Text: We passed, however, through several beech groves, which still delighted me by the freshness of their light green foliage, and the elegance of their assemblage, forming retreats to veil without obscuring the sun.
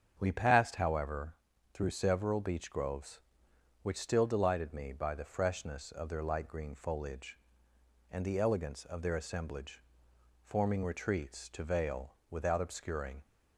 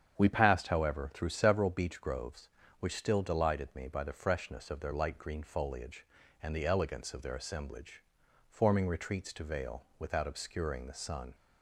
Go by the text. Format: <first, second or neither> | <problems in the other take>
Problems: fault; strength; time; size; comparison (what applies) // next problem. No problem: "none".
second | starts louder than the rest; strong; until 1.2 s; 8 dB; strong in the second // stops before "the sun"; at 13.2 s